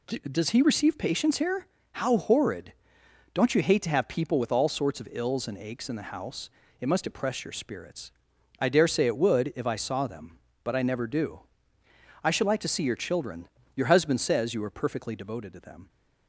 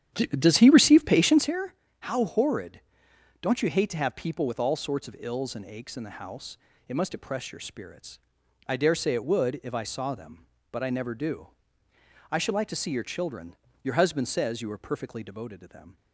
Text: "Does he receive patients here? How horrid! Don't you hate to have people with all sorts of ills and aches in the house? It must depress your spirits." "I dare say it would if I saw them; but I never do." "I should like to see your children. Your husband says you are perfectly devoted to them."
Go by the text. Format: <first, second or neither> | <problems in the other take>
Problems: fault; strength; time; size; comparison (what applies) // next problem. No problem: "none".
first | starts louder than the rest; strong; until 1.5 s; 9.5 dB